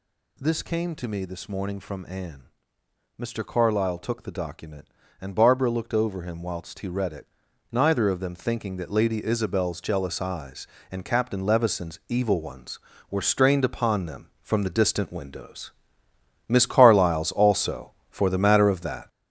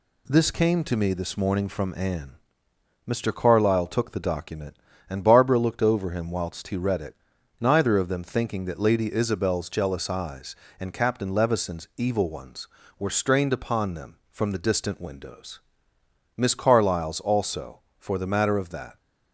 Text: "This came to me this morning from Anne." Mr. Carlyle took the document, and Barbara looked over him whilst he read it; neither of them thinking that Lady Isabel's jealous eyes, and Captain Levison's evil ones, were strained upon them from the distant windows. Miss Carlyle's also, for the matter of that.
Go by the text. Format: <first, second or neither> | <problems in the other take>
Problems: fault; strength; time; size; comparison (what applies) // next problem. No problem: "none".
second | gets louder; throughout; 6 dB